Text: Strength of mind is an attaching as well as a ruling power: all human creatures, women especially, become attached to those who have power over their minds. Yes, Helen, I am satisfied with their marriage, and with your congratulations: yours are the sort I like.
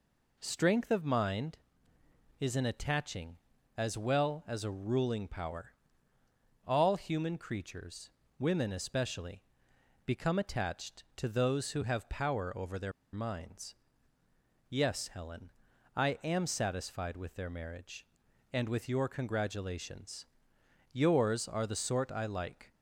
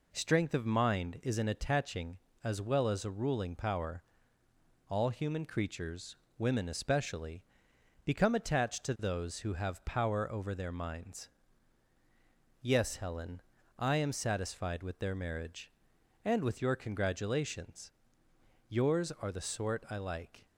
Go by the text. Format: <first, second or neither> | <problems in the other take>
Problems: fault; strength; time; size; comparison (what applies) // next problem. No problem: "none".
second | pauses between "their" and "minds"; slight; at 12.9 s; 0.22 s long